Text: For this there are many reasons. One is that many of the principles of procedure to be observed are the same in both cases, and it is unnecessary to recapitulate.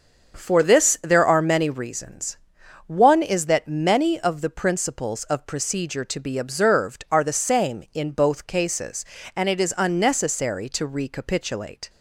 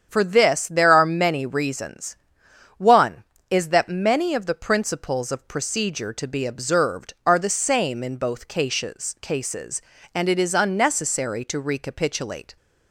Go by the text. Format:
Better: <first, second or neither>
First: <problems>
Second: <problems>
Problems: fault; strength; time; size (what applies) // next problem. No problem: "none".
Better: first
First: starts louder than the rest; until 1.4 s; 6.5 dB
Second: starts louder than the rest; strong; until 1.1 s; 8 dB // says "cases" twice; at 9.2 s